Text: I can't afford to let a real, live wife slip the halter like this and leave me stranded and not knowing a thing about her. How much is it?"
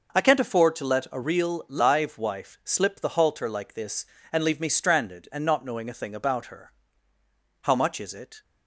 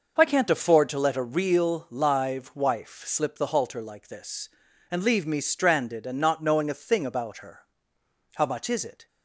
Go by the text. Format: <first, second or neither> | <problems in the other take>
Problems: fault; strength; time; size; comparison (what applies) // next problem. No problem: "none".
neither | none